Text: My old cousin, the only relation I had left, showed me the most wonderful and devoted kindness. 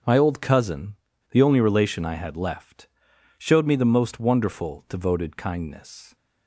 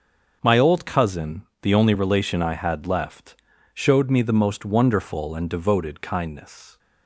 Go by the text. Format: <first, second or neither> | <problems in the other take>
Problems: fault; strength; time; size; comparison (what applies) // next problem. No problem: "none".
second | starts louder than the rest; noticeable; until 1.3 s; 6 dB; also in the second // skips "and"; at 4.8 s